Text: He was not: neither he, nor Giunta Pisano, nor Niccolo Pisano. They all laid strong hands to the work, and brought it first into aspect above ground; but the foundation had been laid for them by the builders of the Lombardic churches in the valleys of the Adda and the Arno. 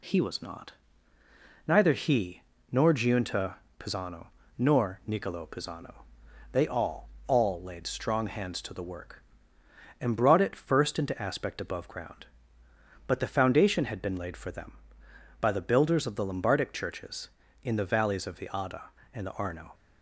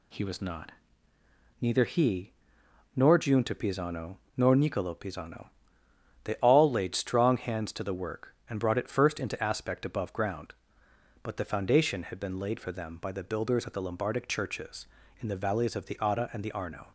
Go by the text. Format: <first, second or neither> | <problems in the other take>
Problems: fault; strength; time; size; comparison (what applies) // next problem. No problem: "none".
second | pauses between "Giunta" and "Pisano"; slight; at 3.5 s; 0.24 s long // says "all" twice; at 7.2 s